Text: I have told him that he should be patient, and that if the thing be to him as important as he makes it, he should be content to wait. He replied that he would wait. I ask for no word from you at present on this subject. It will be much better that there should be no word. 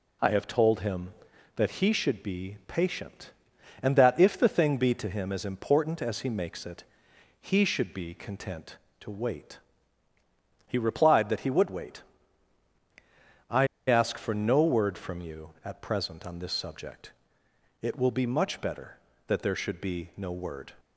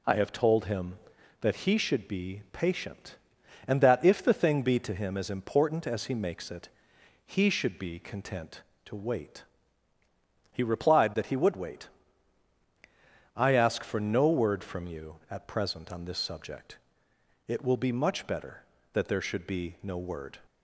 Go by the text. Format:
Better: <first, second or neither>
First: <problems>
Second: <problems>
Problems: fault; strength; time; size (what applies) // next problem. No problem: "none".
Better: second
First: pauses between "I" and "ask"; slight; at 13.6 s; 0.20 s long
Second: none